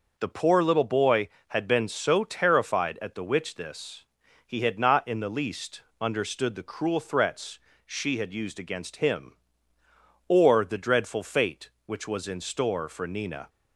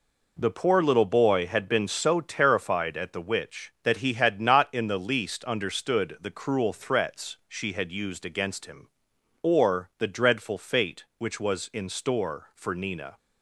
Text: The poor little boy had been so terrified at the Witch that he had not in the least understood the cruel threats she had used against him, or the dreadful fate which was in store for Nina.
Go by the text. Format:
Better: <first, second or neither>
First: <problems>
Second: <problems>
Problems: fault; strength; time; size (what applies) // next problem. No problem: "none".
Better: second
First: says "this" for "that"; at 3.5 s // pauses between "least" and "understood"; slight; at 5.8 s; 0.18 s long // pauses between "threats" and "she"; slight; at 7.5 s; 0.26 s long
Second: none